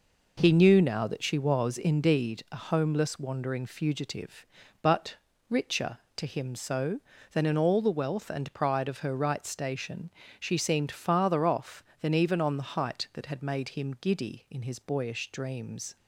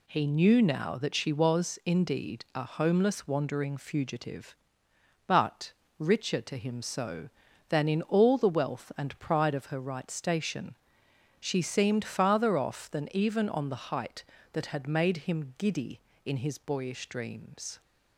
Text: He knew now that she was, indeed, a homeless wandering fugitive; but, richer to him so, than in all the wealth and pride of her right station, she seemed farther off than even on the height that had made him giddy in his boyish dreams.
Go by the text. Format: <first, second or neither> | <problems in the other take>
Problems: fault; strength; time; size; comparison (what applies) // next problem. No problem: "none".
neither | none